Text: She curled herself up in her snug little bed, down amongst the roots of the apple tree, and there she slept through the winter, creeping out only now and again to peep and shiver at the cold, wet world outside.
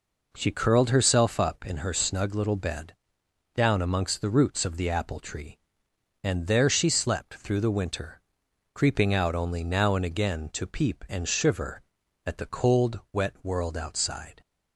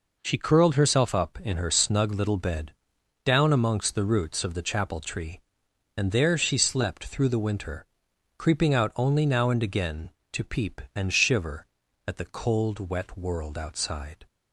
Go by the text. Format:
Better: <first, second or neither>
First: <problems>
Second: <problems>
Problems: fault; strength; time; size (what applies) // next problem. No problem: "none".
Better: first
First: none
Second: says "chapel" for "apple"; at 4.6 s